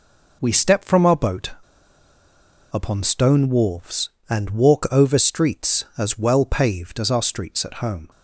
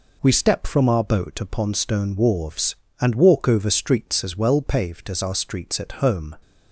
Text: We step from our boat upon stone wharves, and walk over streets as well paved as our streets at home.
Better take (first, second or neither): second